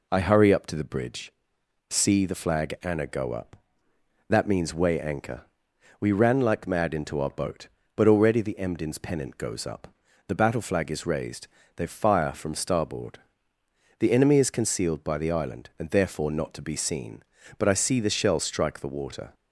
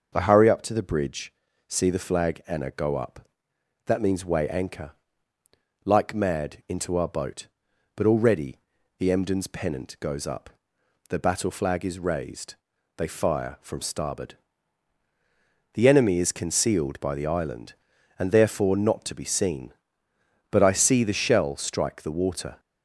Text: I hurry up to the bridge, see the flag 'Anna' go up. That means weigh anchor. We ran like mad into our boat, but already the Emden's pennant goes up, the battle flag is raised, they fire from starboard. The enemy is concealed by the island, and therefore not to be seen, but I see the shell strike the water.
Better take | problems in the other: first | skips "We ran"; at 5.3 s // pauses between "already" and "the"; at 8.5 s; 0.42 s long

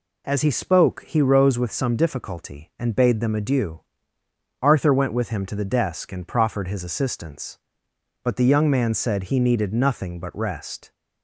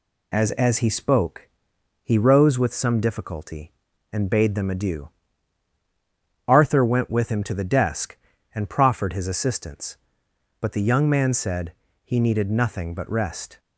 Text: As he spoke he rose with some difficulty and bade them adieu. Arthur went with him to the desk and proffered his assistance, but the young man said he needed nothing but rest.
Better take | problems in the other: first | says "As" twice; at 0.5 s // pauses between "spoke" and "he"; noticeable; at 1.4 s; 0.56 s long // pauses between "said" and "he"; slight; at 11.7 s; 0.32 s long

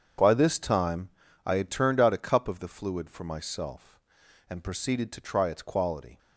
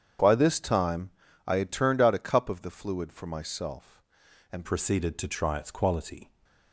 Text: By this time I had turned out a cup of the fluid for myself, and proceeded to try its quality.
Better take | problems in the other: first | starts louder than the rest; strong; until 1.5 s; 8 dB; strong in the first // pauses between "time" and "I"; at 1.0 s; 0.38 s long; also in the first // changes voice at "proceeded"; from 4.6 s on; 1.6 s long

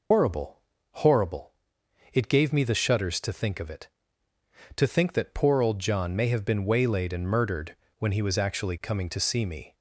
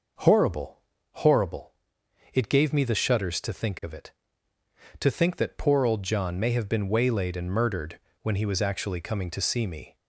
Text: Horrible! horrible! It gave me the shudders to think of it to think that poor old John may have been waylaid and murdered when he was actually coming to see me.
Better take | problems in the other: second | loses the start of "Horrible"; at 0.1 s; 130 ms // pauses between "murdered" and "when"; slight; at 7.7 s; 0.24 s long; slight in the second

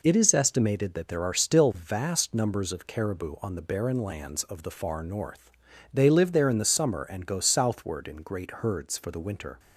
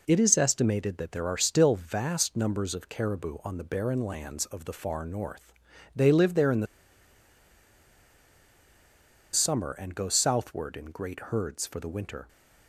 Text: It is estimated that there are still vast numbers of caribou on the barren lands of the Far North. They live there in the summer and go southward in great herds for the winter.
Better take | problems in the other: first | pauses between "the" and "summer"; strong; at 6.6 s; 2.6 s long

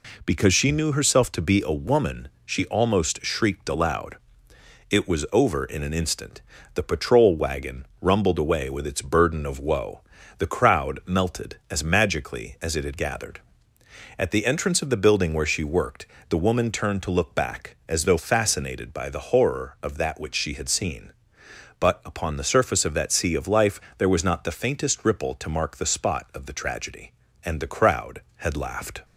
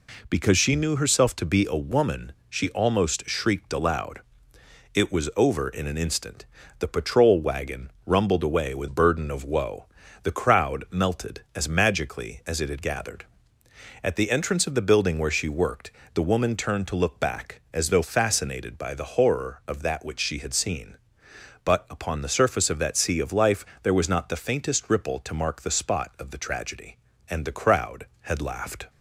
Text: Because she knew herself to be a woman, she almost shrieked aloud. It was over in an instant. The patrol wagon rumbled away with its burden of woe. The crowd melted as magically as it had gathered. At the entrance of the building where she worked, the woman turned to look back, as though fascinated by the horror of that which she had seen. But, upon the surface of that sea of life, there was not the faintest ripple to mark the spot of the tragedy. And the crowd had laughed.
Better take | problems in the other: first | skips "its"; at 8.8 s

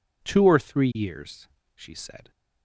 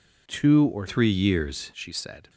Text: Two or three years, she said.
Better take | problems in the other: first | changes voice from "three" to "years"; from 0.8 to 1.7 s; 0.9 s long

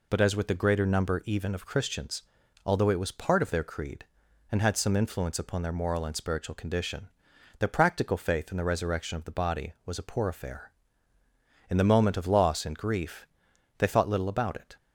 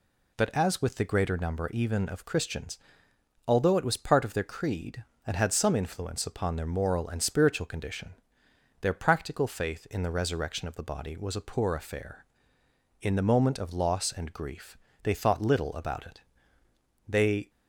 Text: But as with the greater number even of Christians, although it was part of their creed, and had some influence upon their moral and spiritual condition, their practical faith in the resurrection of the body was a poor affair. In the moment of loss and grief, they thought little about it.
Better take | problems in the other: first | goes on to say "They"; slight; from 17.0 s on; 0.42 s long

